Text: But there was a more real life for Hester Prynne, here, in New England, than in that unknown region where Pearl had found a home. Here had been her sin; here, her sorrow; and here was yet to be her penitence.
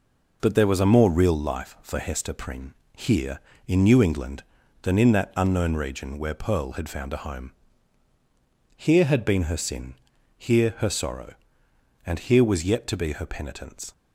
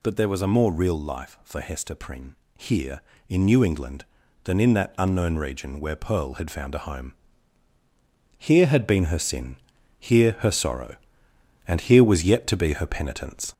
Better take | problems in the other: first | gets louder; throughout; 4 dB

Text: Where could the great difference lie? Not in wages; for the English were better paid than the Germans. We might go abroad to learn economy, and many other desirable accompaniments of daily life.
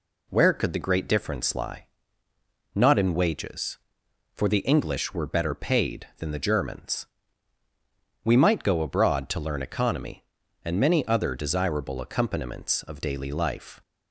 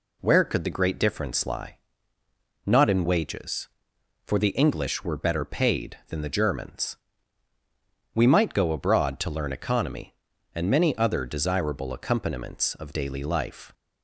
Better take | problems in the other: neither | none

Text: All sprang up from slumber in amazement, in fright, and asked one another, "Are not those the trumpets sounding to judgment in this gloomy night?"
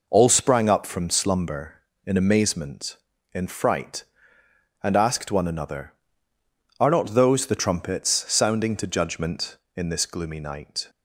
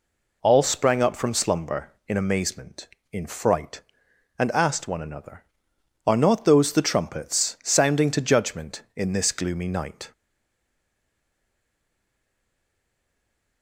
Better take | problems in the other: first | stays silent after the last word; strong; from 10.1 s on; 3.5 s long

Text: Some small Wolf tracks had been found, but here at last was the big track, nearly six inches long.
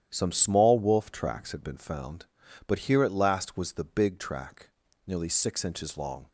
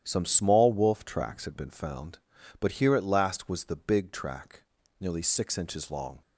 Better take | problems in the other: neither | starts louder than the rest; strong; the same in both

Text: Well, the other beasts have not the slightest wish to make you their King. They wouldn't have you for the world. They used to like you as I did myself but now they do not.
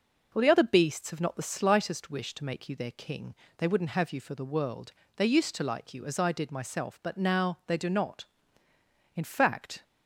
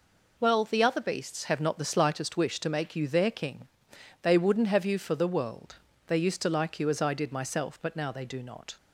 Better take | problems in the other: second | goes on to say "In fact"; noticeable; from 9.1 s on; 0.68 s long

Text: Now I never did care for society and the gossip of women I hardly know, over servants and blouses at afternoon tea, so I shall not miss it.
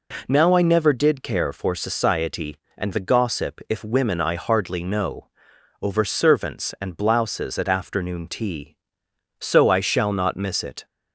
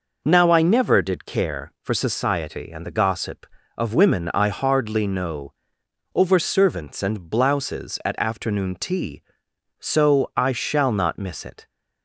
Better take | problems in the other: second | says "if" for "of"; at 3.6 s

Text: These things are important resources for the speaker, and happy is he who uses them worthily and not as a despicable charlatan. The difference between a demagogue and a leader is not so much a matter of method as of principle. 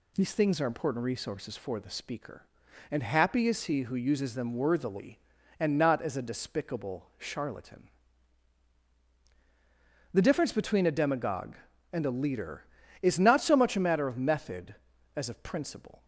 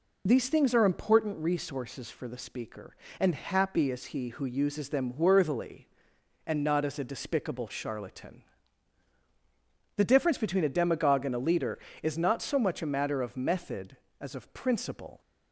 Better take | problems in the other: first | loses the start of "These"; at 0.2 s; 30 ms

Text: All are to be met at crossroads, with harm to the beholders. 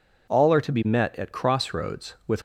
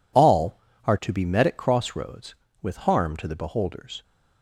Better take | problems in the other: second | stops before "harm to the beholders"; at 2.3 s

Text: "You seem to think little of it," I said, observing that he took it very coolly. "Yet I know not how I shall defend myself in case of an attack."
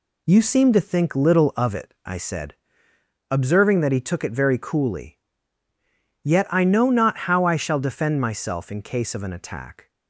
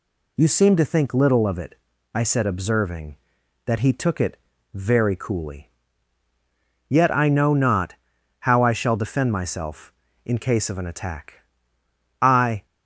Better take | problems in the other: first | pauses between "it" and "very"; slight; at 4.3 s; 0.36 s long // pauses between "not" and "how"; at 7.9 s; 0.44 s long // goes on to say "I"; slight; from 12.2 s on; 0.44 s long

